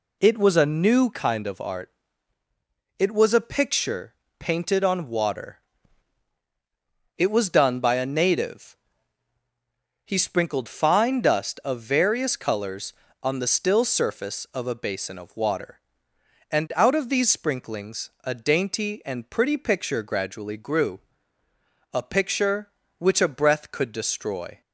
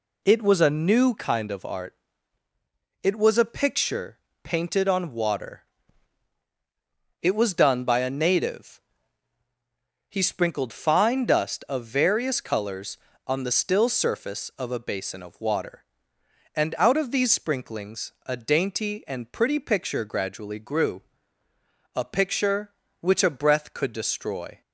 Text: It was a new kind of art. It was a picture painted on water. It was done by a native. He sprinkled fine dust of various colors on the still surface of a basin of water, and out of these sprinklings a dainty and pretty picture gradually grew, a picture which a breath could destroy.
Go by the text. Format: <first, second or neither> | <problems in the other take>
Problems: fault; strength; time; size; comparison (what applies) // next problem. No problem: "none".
neither | pauses between "picture" and "painted"; slight; the same in both